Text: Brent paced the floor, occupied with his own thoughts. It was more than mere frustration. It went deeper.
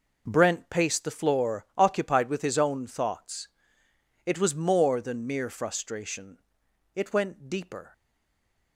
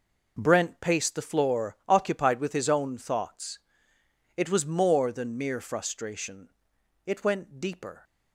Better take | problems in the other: second | stays silent after the last word; slight; from 7.9 s on; 0.8 s long

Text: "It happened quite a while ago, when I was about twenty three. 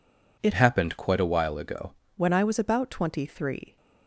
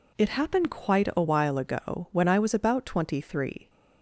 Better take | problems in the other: second | changes voice from "happened" to "ago"; from 0.5 to 1.9 s; 1.4 s long

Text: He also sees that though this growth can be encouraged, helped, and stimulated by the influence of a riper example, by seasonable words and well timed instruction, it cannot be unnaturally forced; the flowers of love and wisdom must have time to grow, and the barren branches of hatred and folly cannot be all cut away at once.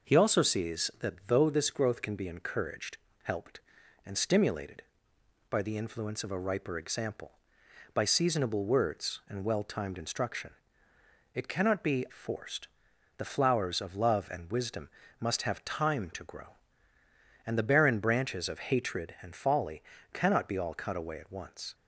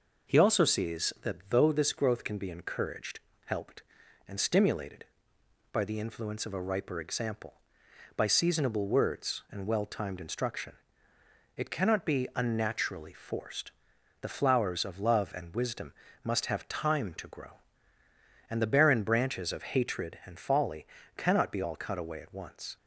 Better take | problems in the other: second | skips "unnaturally"; at 12.0 s // pauses between "wisdom" and "must"; slight; at 14.9 s; 0.28 s long; slight in the second // pauses between "folly" and "cannot"; slight; at 19.8 s; 0.32 s long; slight in the second

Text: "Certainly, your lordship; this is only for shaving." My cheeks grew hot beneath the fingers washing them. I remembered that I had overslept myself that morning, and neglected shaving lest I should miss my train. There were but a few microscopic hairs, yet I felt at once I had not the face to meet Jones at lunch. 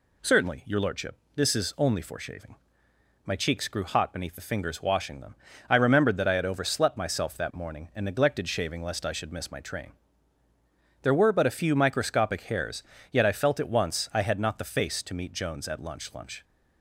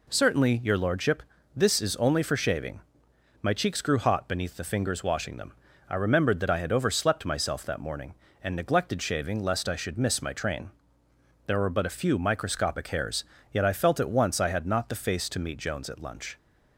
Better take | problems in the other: second | says "lunch" twice; at 16.1 s

